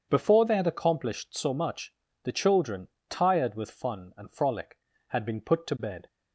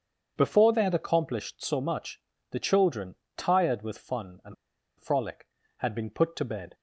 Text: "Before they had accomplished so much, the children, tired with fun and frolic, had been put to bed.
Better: first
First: starts louder than the rest; strong; until 1.1 s; 7 dB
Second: starts louder than the rest; strong; until 1.3 s; 7 dB // pauses between "and" and "frolic"; at 4.5 s; 0.45 s long

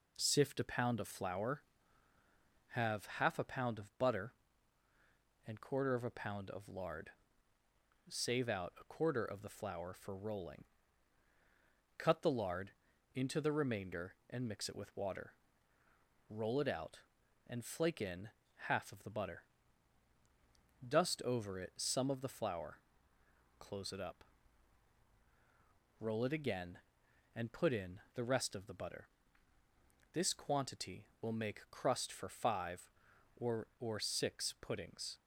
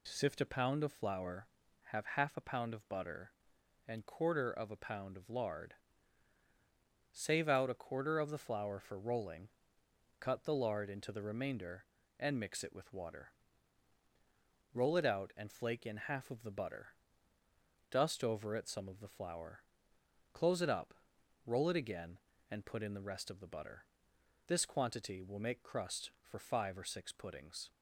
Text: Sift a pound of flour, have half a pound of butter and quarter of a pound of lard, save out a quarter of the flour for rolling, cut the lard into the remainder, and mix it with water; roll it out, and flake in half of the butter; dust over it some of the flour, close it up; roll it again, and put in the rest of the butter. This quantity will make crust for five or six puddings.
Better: second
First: pauses between "lard" and "into"; at 12.7 s; 0.44 s long // pauses between "in" and "half"; at 18.2 s; 0.40 s long // says "or" twice; at 33.7 s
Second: none

